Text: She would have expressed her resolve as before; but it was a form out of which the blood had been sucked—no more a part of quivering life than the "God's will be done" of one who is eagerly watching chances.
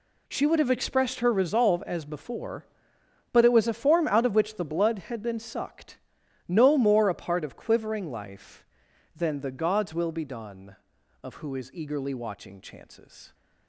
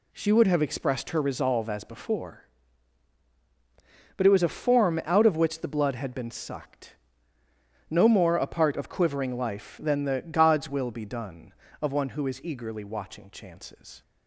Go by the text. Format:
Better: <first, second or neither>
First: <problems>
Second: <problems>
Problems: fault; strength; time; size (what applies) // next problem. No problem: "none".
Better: second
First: skips "one"; at 11.3 s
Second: none